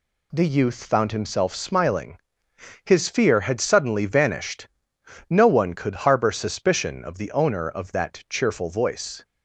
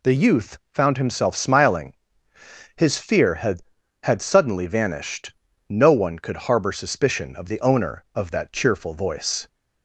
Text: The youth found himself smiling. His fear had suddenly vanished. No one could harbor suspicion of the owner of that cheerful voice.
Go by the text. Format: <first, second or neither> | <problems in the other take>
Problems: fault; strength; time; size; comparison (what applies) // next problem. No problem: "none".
first | says "had" twice; at 4.0 s